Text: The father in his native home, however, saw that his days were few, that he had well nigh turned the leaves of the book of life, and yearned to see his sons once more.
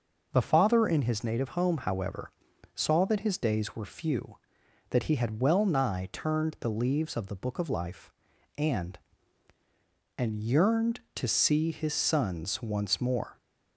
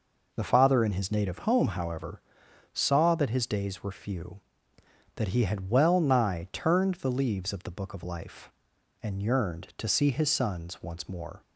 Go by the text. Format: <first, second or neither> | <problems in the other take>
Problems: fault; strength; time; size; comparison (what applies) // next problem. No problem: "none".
second | says "and" twice; at 10.1 s